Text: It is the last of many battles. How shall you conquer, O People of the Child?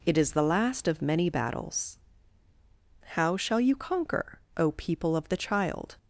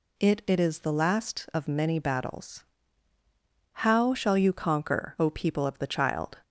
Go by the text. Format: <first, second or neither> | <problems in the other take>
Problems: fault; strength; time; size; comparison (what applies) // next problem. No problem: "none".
first | says "It" twice; at 0.4 s